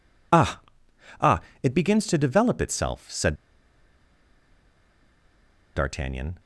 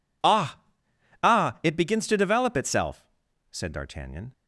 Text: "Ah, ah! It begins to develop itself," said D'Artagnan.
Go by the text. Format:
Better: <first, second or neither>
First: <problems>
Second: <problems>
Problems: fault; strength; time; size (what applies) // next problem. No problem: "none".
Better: second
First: pauses between "said" and "D'Artagnan"; strong; at 3.3 s; 2.3 s long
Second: none